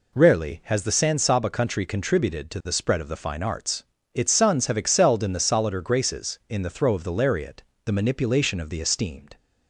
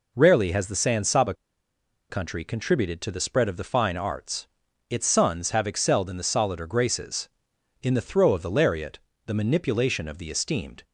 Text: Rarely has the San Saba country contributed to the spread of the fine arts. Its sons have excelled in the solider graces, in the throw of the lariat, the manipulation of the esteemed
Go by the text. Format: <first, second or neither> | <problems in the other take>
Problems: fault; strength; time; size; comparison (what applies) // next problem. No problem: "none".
first | pauses between "Saba" and "country"; noticeable; at 1.3 s; 0.76 s long